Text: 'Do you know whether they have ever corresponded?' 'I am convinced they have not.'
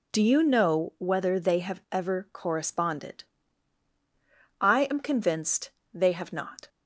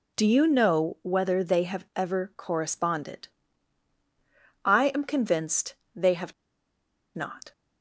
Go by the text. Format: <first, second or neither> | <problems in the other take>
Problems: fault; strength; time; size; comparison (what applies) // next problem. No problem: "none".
first | pauses between "convinced" and "they"; slight; at 5.7 s; 0.22 s long; slight in the first // pauses between "have" and "not"; noticeable; at 6.3 s; 0.84 s long